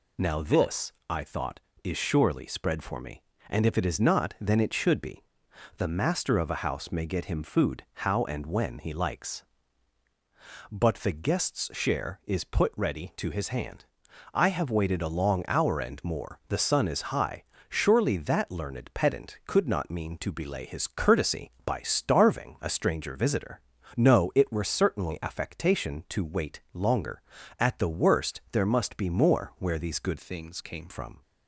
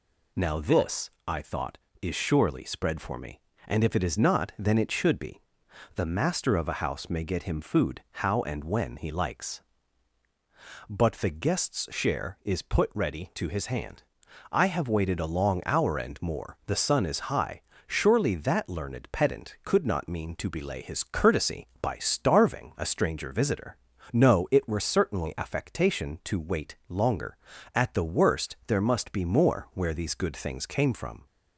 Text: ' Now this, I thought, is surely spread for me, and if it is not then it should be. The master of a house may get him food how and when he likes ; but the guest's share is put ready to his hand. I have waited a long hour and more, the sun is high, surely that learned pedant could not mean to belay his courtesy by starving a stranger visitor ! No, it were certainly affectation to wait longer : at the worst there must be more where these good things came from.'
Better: second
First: changes voice from "things" to "came"; from 30.1 to 30.8 s; 0.7 s long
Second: none

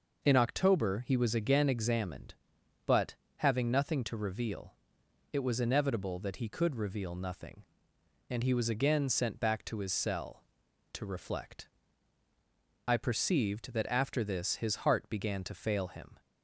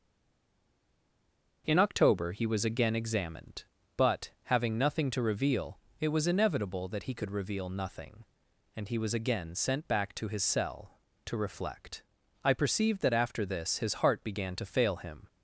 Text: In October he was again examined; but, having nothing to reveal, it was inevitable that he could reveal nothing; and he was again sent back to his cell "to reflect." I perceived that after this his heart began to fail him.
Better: first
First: none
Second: stays silent before the first word; noticeable; until 1.6 s; 1.6 s long

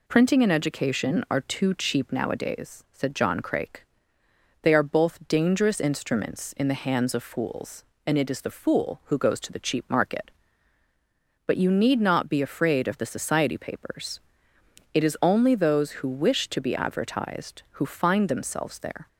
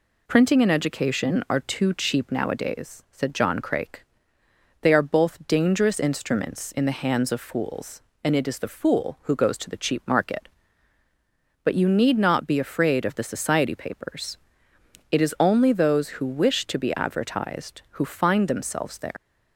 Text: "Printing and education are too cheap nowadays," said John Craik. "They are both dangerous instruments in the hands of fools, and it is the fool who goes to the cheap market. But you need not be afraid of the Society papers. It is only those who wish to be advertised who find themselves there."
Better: first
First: none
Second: leaves "there" unfinished; at 19.1 s; 100 ms

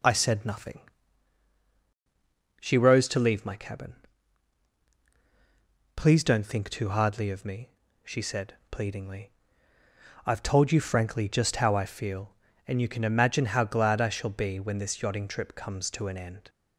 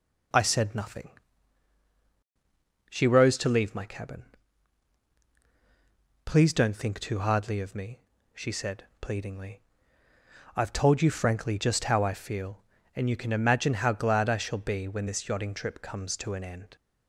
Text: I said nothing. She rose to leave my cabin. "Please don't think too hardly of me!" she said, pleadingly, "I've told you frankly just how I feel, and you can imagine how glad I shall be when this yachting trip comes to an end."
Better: neither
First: none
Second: none

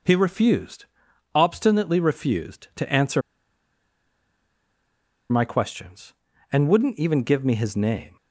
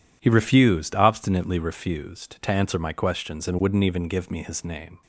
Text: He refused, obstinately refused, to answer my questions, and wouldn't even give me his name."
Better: second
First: pauses between "answer" and "my"; strong; at 3.2 s; 2.0 s long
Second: none

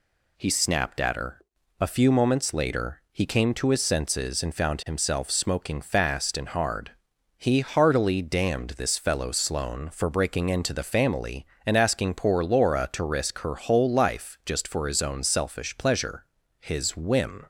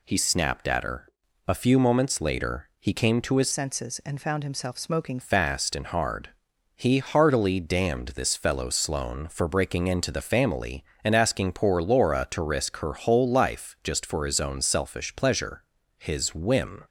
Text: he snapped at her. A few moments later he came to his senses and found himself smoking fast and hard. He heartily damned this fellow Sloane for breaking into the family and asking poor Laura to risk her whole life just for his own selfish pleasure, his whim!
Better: first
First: none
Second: changes voice from "senses" to "smoking"; from 3.5 to 5.1 s; 1.6 s long

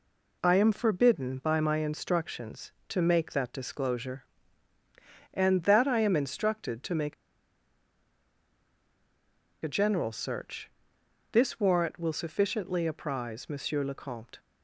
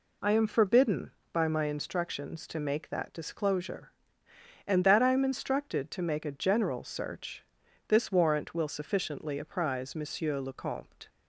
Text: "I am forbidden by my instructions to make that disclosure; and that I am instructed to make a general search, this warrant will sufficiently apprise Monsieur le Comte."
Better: second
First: pauses between "make" and "a"; strong; at 7.1 s; 2.5 s long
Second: none

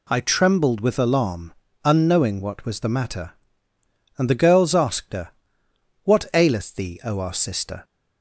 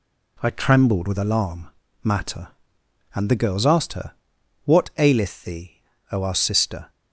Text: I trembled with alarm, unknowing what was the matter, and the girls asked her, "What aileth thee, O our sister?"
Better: first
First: none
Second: skips "unknowing what was the"; at 1.8 s

